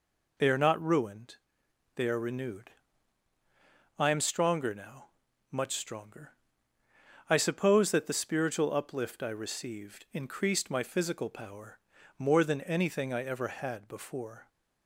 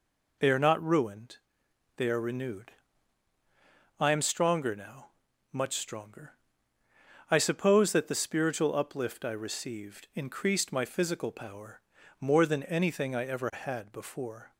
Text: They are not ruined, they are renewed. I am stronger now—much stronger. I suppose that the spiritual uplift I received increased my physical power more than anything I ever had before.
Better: neither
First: pauses between "power" and "more"; at 11.7 s; 0.40 s long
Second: pauses between "power" and "more"; at 11.8 s; 0.40 s long

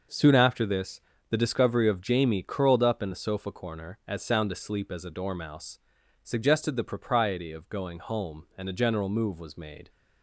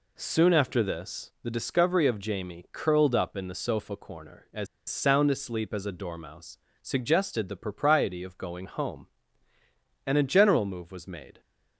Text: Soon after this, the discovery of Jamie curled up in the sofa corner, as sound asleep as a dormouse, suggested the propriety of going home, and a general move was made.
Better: first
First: none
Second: pauses between "as" and "sound"; slight; at 4.6 s; 0.23 s long

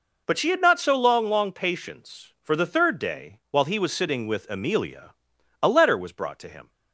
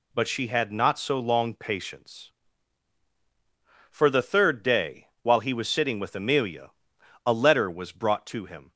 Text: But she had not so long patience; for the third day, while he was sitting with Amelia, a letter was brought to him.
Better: second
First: says "long" twice; at 1.2 s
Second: none

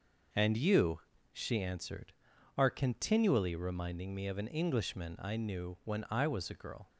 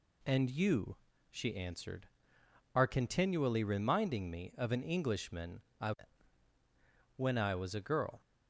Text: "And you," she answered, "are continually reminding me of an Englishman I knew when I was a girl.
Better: first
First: none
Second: pauses between "Englishman" and "I"; slight; at 5.6 s; 0.18 s long // skips "knew"; at 6.5 s

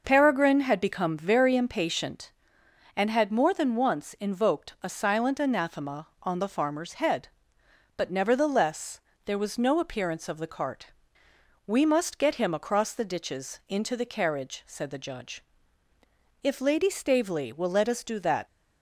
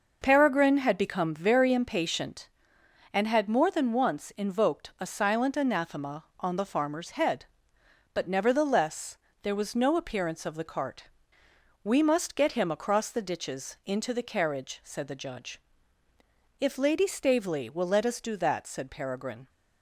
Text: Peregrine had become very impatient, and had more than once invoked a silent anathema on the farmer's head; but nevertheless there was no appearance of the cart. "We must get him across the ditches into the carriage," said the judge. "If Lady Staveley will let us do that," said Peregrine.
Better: second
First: pauses between "nevertheless" and "there"; slight; at 8.9 s; 0.26 s long // stops before "said Peregrine"; at 18.4 s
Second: pauses between "nevertheless" and "there"; slight; at 9.1 s; 0.26 s long

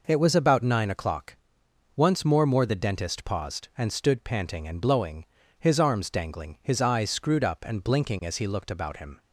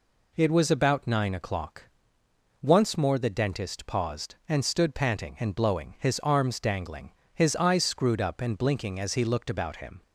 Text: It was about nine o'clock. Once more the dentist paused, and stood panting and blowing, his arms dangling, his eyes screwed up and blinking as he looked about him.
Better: second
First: says "more" twice; at 2.4 s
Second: none

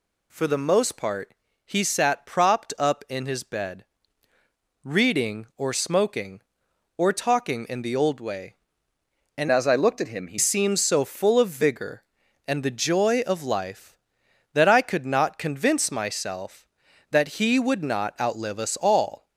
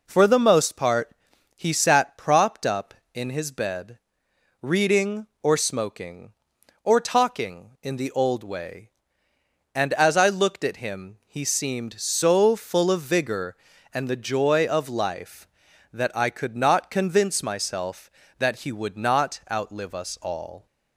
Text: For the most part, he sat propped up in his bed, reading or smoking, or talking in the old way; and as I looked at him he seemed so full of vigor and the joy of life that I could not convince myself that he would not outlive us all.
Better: second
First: changes voice from "as" to "he"; from 9.5 to 10.3 s; 0.8 s long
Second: none

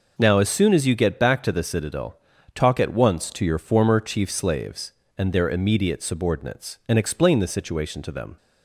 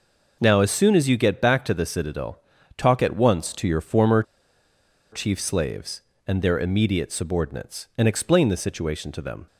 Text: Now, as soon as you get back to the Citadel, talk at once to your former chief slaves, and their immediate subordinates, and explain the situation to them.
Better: first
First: none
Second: pauses between "former" and "chief"; noticeable; at 4.2 s; 0.88 s long

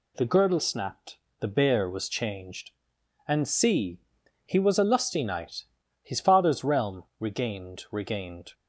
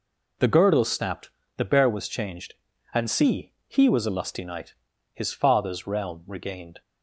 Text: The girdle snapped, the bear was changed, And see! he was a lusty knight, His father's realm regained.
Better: second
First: pauses between "realm" and "regained"; slight; at 7.0 s; 0.16 s long // says "regained" twice; at 7.9 s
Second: none

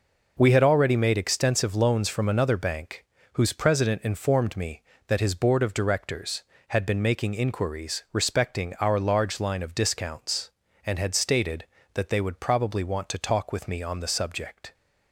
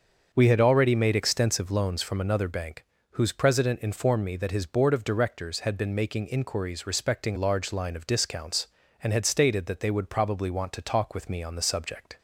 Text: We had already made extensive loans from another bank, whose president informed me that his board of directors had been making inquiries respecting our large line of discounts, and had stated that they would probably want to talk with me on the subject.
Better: first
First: none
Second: starts louder than the rest; until 1.3 s; 6.5 dB // skips "our"; at 7.3 s

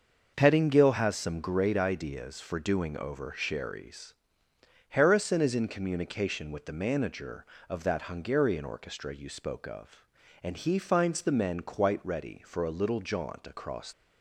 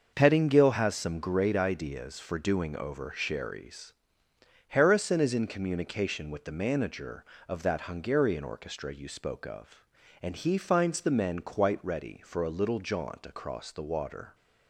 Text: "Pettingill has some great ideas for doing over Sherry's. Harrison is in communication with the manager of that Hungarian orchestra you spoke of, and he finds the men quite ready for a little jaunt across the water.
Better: second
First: starts louder than the rest; until 1.3 s; 6.5 dB // stops before "the water"; at 13.9 s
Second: starts louder than the rest; until 1.1 s; 6.5 dB

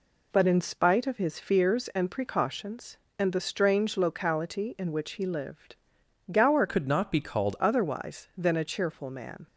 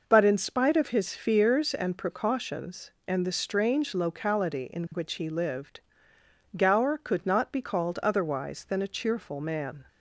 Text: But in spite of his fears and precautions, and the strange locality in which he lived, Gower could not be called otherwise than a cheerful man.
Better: second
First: changes voice from "could" to "called"; from 6.6 to 7.5 s; 0.9 s long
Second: none

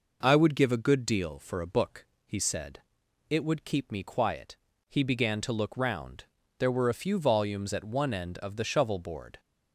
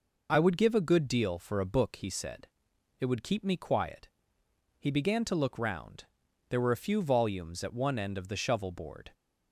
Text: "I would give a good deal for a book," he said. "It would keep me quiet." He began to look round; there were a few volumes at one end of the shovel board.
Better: neither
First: none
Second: none

